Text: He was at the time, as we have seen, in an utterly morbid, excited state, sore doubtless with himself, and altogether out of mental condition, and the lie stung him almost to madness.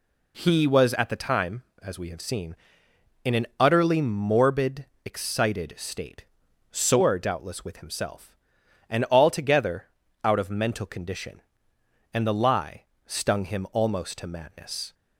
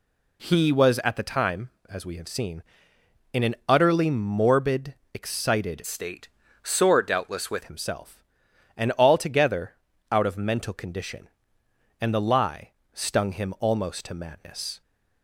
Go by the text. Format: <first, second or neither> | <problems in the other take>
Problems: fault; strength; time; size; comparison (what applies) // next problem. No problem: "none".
first | changes voice from "state" to "with"; from 5.8 to 7.6 s; 1.8 s long // pauses between "altogether" and "out"; slight; at 9.7 s; 0.36 s long; slight in the first // pauses between "lie" and "stung"; slight; at 12.7 s; 0.22 s long; slight in the first